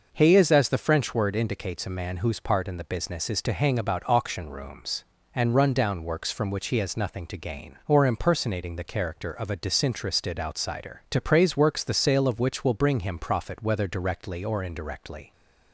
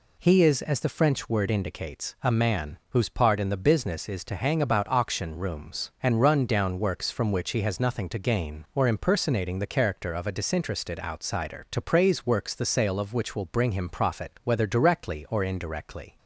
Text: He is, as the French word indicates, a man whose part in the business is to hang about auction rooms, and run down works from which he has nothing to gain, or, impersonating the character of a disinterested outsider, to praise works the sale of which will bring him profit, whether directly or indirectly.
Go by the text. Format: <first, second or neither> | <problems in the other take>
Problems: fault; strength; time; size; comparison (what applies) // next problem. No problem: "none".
neither | none